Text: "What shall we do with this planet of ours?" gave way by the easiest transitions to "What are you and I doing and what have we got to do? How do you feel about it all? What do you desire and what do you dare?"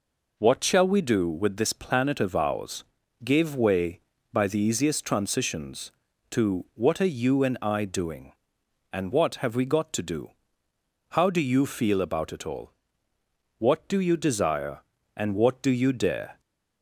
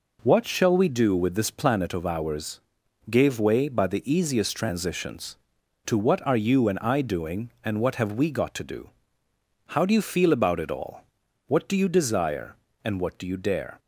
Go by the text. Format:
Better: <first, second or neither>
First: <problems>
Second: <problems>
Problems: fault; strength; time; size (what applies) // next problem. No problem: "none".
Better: neither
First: none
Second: none